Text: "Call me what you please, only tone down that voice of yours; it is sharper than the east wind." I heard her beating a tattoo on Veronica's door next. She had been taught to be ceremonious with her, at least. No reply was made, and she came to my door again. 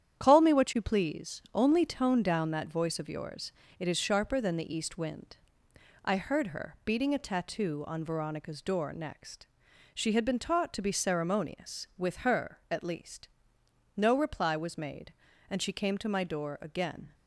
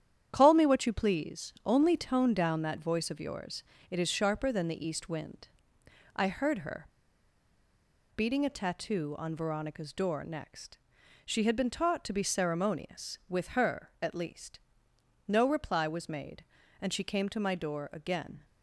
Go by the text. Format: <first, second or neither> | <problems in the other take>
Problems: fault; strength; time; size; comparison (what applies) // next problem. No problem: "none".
first | starts louder than the rest; strong; until 1.3 s; 9.5 dB; strong in the first // pauses between "her" and "beating"; strong; at 6.8 s; 1.2 s long